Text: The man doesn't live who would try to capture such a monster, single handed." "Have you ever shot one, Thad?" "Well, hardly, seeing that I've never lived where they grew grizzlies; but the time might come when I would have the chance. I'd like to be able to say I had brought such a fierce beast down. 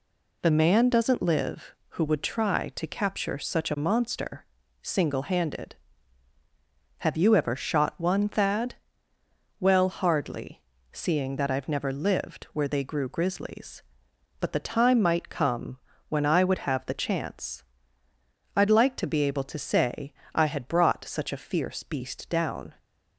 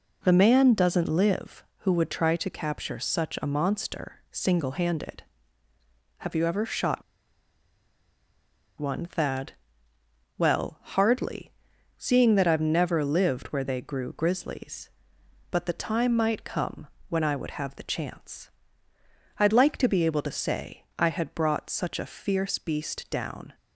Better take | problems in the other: first | pauses between "shot" and "one"; strong; at 7.0 s; 1.7 s long // pauses between "come" and "when"; slight; at 16.8 s; 0.22 s long; slight in the first // pauses between "say" and "I"; slight; at 20.8 s; 0.16 s long; slight in the first

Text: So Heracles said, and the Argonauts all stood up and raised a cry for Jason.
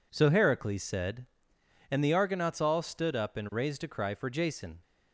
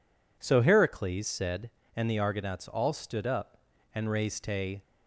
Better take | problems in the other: first | stops before "cry for Jason"; at 4.8 s

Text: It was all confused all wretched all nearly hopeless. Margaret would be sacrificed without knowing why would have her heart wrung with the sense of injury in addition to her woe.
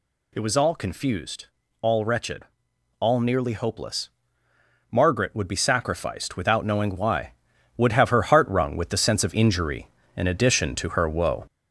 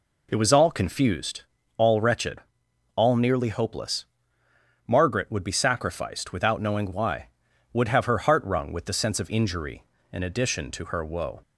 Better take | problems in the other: second | gets louder; noticeable; throughout; 4.5 dB // pauses between "confused" and "all"; slight; at 1.4 s; 0.34 s long; slight in the second // pauses between "wretched" and "all"; noticeable; at 2.4 s; 0.54 s long; noticeable in the second

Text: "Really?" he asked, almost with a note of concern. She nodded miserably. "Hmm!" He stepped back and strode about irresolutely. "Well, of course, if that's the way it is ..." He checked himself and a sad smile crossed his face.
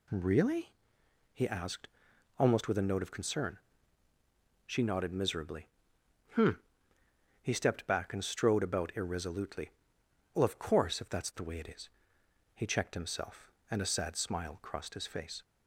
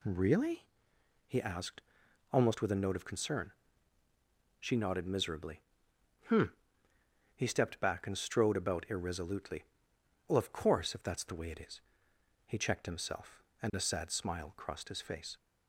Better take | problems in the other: neither | none

